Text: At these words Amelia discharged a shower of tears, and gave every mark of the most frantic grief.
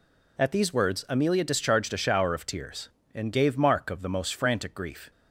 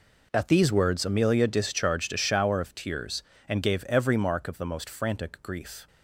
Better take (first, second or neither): second